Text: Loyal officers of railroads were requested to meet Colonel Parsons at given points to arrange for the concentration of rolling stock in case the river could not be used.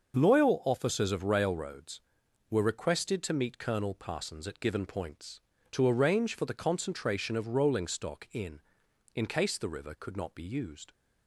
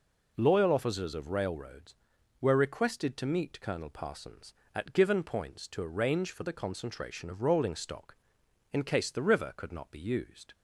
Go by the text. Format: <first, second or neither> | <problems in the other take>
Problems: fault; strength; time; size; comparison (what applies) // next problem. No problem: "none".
second | starts louder than the rest; noticeable; until 1.1 s; 6 dB // says "in" twice; at 9.1 s